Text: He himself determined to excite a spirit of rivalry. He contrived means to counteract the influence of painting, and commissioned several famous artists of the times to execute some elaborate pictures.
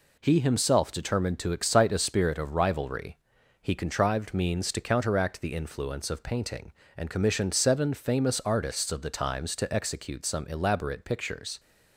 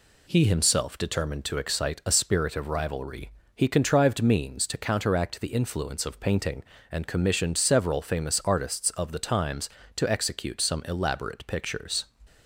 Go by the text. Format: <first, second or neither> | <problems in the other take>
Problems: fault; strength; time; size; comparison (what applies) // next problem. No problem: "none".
second | says "seven" for "several"; at 7.5 s